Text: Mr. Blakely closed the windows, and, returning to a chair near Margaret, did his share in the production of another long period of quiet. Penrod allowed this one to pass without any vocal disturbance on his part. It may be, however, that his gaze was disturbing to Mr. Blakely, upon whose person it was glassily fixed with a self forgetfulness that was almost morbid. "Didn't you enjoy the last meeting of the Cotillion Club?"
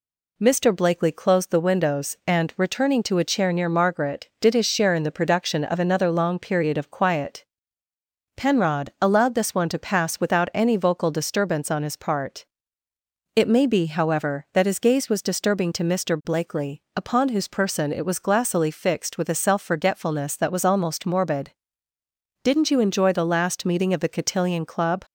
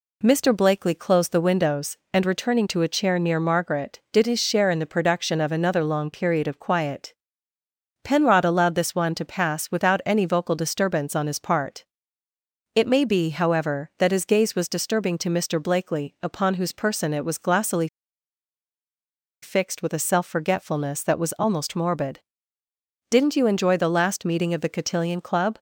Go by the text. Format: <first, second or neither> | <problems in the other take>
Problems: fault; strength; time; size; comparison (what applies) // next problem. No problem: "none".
first | pauses between "glassily" and "fixed"; strong; at 17.8 s; 1.5 s long